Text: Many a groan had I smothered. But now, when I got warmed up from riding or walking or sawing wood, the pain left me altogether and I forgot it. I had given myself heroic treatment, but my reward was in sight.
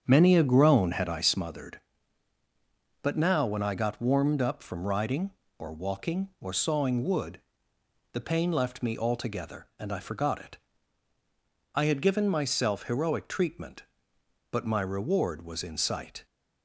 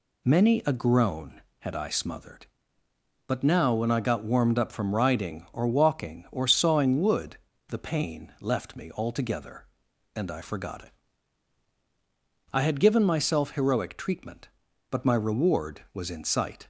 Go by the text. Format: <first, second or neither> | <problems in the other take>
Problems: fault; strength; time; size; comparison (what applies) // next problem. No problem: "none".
second | starts louder than the rest; strong; until 1.4 s; 7.5 dB